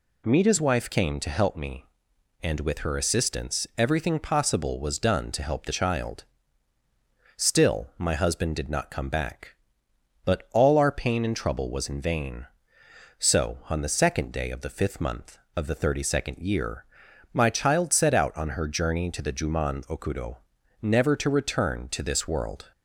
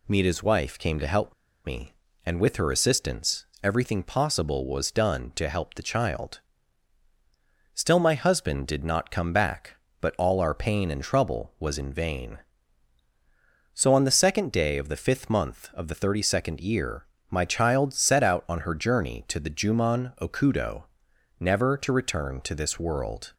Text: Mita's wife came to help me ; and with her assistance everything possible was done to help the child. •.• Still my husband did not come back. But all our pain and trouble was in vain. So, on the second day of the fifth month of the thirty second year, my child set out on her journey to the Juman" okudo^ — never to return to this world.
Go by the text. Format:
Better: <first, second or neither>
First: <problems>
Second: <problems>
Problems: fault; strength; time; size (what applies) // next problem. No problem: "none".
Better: first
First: none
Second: pauses between "help" and "me"; slight; at 1.3 s; 0.32 s long // pauses between "assistance" and "everything"; slight; at 3.4 s; 0.18 s long